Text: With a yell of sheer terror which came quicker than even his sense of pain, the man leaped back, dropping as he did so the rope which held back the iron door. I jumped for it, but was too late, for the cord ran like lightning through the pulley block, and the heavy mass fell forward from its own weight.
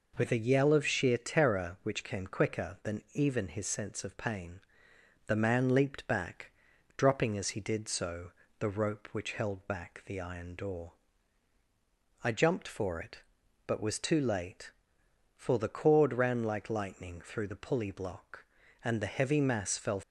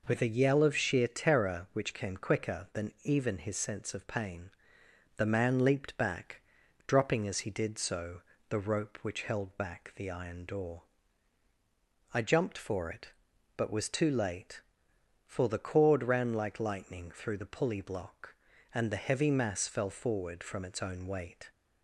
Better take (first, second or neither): second